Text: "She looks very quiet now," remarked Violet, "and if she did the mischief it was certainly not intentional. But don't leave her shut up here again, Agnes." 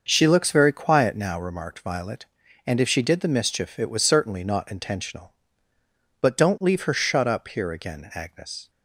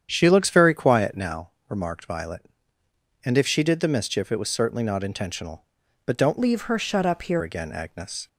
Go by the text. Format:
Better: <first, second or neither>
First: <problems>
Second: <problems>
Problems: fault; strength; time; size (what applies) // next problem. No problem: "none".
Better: first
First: starts louder than the rest; until 1.0 s; 6.5 dB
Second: starts louder than the rest; strong; until 1.1 s; 8.5 dB // changes voice from "leave" to "here"; from 6.3 to 7.4 s; 1.1 s long